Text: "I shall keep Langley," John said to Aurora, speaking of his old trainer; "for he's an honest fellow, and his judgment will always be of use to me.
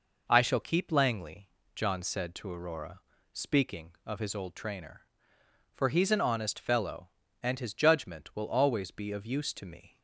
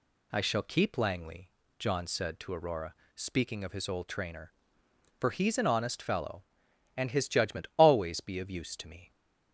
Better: first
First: none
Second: skips "will"; at 7.7 s

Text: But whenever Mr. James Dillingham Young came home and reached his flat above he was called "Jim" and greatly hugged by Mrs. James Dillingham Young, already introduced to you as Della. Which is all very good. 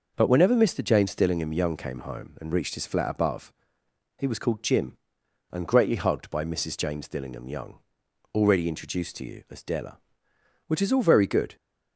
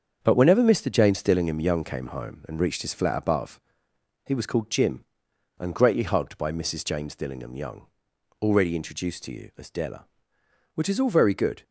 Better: first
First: pauses between "above" and "he"; noticeable; at 3.5 s; 0.68 s long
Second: gets quieter; throughout; 7 dB // pauses between "above" and "he"; noticeable; at 3.5 s; 0.68 s long

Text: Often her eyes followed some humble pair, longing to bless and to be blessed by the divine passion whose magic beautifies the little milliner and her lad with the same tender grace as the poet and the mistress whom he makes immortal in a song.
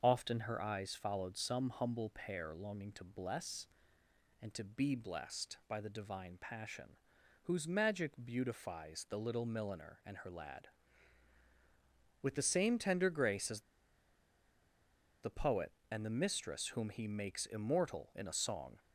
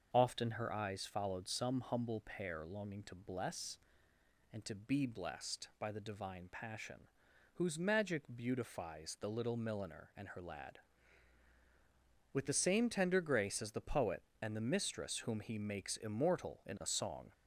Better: second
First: starts louder than the rest; until 1.0 s; 6.5 dB // pauses between "passion" and "whose"; noticeable; at 6.9 s; 0.48 s long // pauses between "as" and "the"; strong; at 13.6 s; 1.6 s long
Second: starts louder than the rest; until 1.1 s; 6.5 dB // pauses between "passion" and "whose"; noticeable; at 7.0 s; 0.48 s long

